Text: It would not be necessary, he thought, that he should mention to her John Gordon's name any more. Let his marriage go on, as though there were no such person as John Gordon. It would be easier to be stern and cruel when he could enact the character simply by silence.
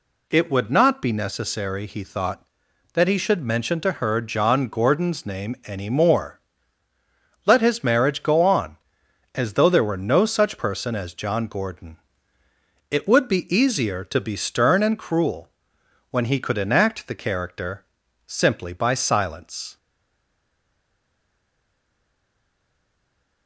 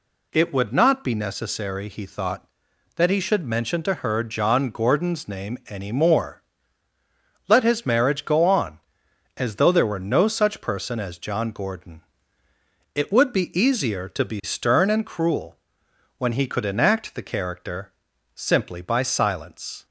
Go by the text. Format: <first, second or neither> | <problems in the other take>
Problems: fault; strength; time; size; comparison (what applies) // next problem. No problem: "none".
second | pauses between "cruel" and "when"; noticeable; at 15.4 s; 0.60 s long; noticeable in the second // pauses between "character" and "simply"; at 17.8 s; 0.43 s long; also in the second // stays silent after the last word; strong; from 19.7 s on; 3.7 s long